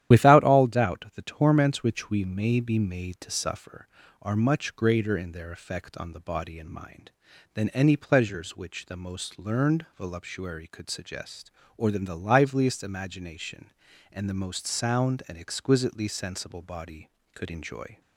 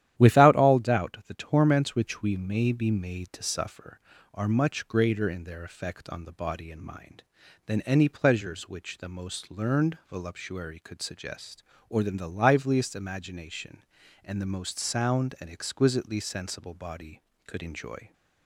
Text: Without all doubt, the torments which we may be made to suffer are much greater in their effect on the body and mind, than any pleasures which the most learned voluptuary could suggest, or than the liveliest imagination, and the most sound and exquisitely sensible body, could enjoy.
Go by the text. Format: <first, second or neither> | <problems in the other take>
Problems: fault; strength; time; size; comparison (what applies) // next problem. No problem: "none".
second | loses the start of "Without"; at 0.1 s; 40 ms // starts louder than the rest; strong; until 1.2 s; 11.5 dB; strong in the second